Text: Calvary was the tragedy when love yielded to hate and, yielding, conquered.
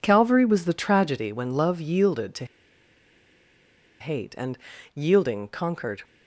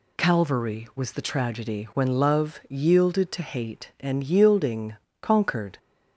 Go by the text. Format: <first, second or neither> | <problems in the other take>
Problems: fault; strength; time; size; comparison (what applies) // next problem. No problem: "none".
second | pauses between "to" and "hate"; strong; at 2.4 s; 1.5 s long